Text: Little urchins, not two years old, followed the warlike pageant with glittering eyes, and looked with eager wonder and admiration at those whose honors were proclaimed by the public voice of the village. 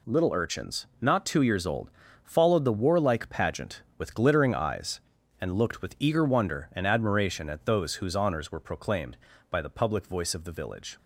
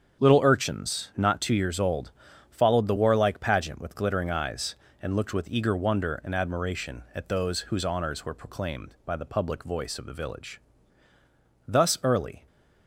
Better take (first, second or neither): first